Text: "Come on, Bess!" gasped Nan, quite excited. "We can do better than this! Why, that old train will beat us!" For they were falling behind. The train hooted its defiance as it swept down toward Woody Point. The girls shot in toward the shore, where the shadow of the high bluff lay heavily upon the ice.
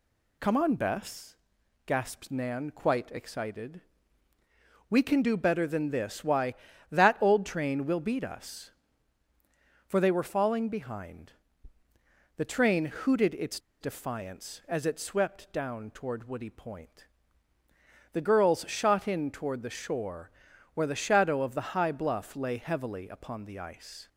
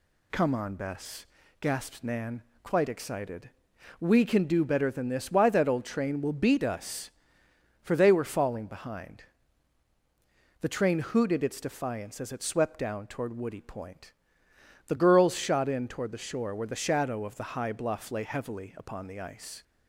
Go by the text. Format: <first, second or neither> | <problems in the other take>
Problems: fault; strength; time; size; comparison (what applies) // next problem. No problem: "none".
second | pauses between "its" and "defiance"; slight; at 13.5 s; 0.22 s long